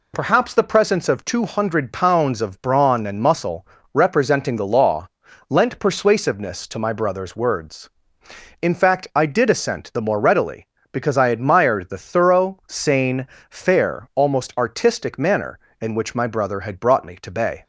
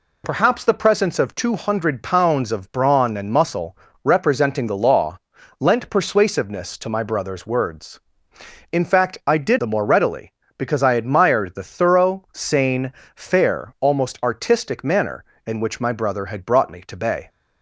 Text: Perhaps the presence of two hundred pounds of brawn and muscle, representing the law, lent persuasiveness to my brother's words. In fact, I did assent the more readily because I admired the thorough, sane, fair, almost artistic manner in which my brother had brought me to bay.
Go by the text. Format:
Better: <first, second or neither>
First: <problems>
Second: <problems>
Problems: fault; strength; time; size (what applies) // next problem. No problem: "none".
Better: first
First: none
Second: skips "assent"; at 9.5 s